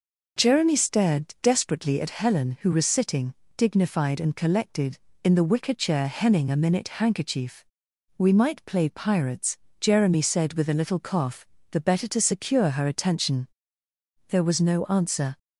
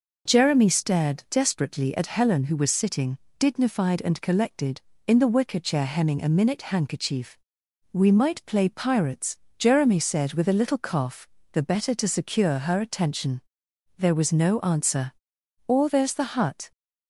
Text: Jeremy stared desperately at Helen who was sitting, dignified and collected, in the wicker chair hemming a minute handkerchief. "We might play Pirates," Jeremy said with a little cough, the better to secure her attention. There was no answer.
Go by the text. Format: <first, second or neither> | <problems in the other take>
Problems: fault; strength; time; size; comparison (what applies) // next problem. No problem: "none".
first | goes on to say "Or there's the hut"; noticeable; from 15.6 s on; 1.0 s long